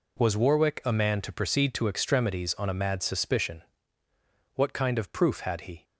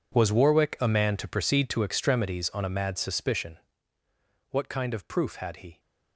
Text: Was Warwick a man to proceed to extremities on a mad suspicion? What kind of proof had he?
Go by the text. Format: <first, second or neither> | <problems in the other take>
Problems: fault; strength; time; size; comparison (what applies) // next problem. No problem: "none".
first | gets quieter; strong; throughout; 15.5 dB